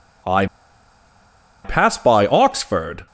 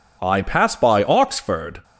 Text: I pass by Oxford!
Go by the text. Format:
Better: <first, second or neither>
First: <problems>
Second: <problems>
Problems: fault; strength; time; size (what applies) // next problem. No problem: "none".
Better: second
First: pauses between "I" and "pass"; at 0.4 s; 1.1 s long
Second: none